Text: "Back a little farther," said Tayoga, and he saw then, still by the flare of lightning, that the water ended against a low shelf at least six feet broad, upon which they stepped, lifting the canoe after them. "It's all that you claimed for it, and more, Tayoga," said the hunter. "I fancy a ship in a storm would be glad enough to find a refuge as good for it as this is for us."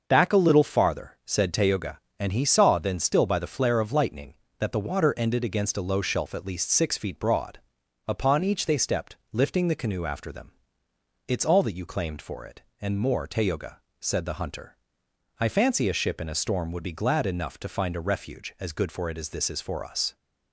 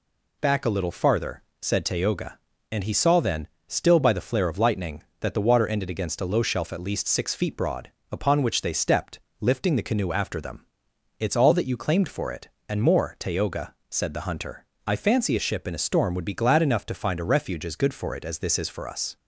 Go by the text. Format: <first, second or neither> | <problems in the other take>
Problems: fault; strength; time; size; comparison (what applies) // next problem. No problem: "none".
second | starts louder than the rest; until 1.0 s; 6 dB // says "each" for "which"; at 8.4 s